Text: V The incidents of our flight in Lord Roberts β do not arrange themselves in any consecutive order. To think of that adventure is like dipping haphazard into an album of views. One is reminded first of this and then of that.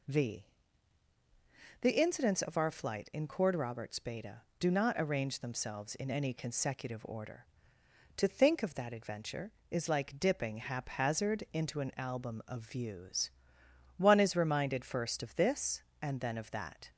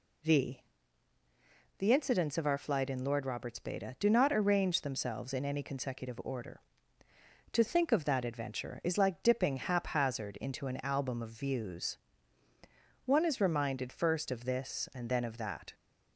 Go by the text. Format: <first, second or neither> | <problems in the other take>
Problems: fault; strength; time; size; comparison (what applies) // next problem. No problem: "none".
second | pauses between "V" and "The"; strong; at 0.4 s; 1.3 s long; also in the second // says "Cord" for "Lord"; at 3.2 s